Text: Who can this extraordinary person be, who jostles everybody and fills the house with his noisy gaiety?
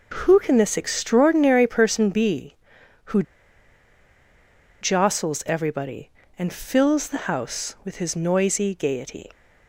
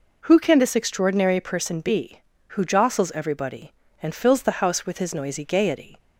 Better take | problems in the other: second | starts louder than the rest; until 1.2 s; 6.5 dB // pauses between "who" and "jostles"; strong; at 3.2 s; 1.5 s long

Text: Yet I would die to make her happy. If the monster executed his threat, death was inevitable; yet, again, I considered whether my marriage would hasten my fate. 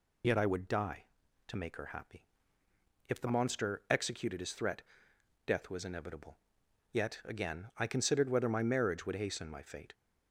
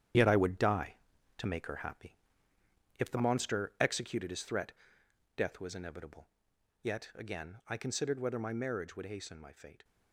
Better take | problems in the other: first | gets quieter; strong; throughout; 9 dB

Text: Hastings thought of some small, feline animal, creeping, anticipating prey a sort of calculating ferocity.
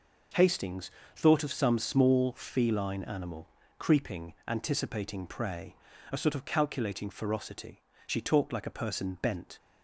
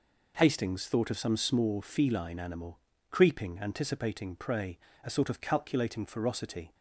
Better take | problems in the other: second | pauses between "Hastings" and "thought"; slight; at 0.9 s; 0.24 s long // pauses between "prey" and "a"; slight; at 5.7 s; 0.36 s long; slight in the second // goes on to say "She talked like a person bent"; from 8.0 s on; 1.5 s long

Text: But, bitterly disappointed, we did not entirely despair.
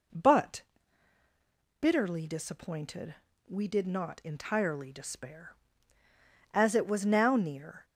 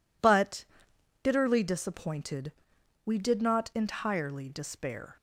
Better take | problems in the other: second | goes on to say "As it was now near"; from 6.5 s on; 1.3 s long

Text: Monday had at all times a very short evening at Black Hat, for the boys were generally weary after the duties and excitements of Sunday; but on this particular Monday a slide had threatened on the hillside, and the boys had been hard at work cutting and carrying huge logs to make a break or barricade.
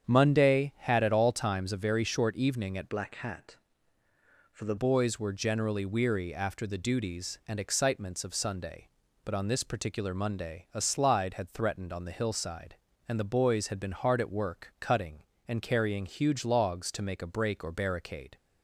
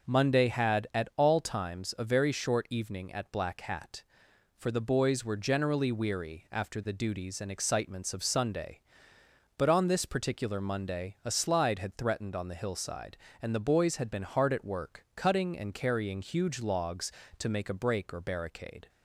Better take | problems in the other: second | starts louder than the rest; strong; until 1.0 s; 8 dB // changes voice from "Black" to "the"; from 2.8 to 4.7 s; 1.9 s long

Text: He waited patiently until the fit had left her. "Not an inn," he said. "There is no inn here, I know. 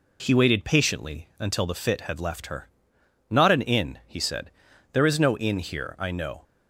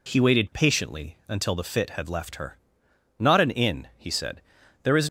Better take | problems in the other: first | stops before "no inn here I know"; at 5.0 s

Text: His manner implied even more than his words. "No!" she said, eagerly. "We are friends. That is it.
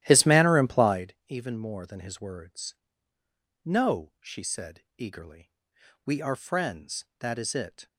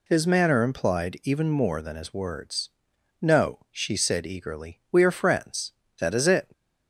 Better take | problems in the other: second | starts louder than the rest; strong; until 1.0 s; 13 dB

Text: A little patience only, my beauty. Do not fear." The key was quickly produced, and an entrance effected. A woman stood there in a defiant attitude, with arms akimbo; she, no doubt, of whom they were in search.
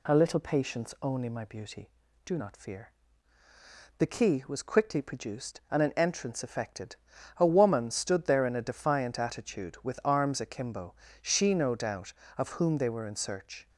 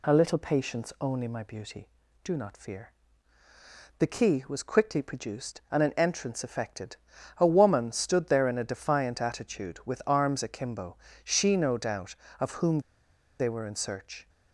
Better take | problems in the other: first | pauses between "whom" and "they"; noticeable; at 12.8 s; 0.58 s long

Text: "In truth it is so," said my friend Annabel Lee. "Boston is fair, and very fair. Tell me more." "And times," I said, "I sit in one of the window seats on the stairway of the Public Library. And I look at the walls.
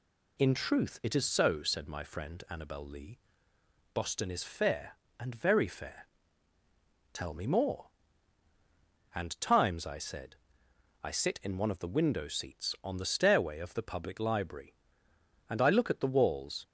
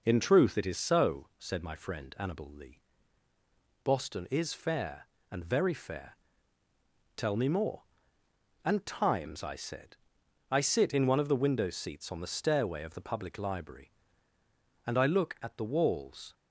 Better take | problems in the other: neither | none

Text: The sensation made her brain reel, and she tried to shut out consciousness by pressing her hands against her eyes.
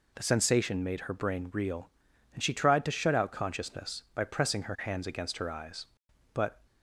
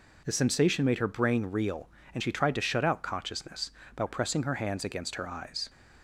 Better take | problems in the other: second | goes on to say "But"; slight; from 6.3 s on; 0.28 s long

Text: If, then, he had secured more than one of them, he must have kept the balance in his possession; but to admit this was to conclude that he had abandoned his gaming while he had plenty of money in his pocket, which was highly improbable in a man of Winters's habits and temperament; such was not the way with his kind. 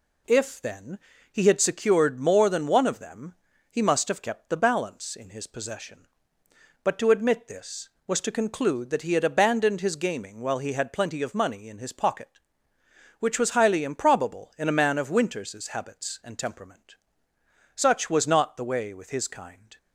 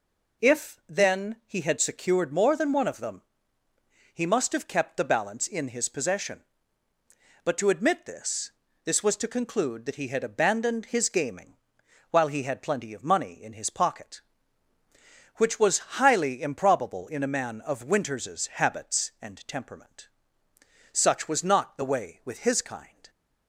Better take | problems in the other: first | says "this" twice; at 8.8 s // pauses between "gaming" and "while"; noticeable; at 11.5 s; 0.56 s long

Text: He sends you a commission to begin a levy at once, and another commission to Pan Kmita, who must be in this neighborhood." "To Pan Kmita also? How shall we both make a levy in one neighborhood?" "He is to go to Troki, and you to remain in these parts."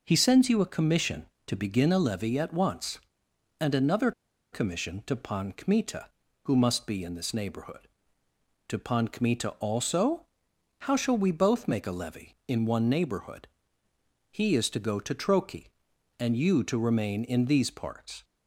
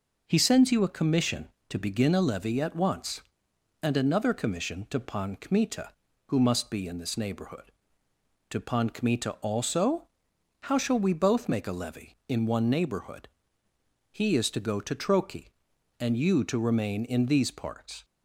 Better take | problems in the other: second | pauses between "another" and "commission"; at 4.1 s; 0.41 s long

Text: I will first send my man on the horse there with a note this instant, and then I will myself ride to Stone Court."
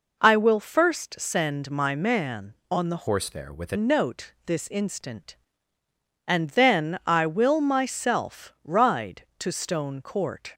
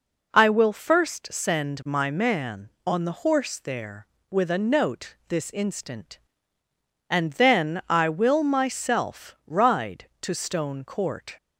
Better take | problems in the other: second | changes voice from "horse" to "a"; from 3.0 to 3.7 s; 0.7 s long

